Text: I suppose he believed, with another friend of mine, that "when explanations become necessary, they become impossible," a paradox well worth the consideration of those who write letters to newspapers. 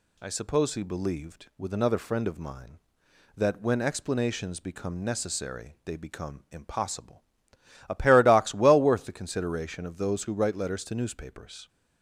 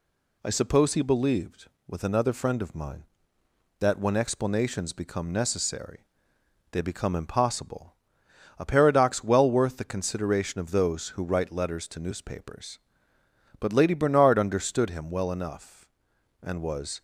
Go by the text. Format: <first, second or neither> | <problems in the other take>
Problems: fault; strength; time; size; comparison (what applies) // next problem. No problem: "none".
first | goes on to say "But Lady Bernard understood him well enough and was"; strong; from 13.5 s on; 3.4 s long